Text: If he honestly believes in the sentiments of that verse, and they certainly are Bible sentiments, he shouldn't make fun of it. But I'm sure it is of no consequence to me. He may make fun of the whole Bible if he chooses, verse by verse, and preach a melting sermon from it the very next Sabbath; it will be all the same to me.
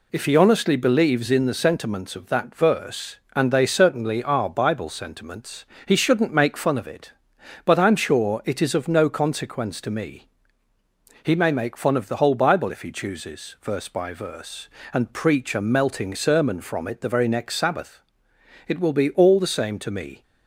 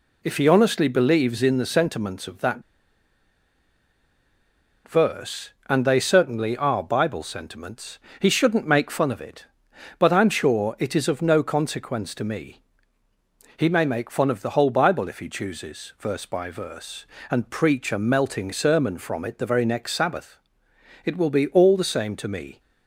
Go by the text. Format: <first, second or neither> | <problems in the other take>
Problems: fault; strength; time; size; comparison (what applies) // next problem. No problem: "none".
first | pauses between "that" and "verse"; strong; at 2.6 s; 2.2 s long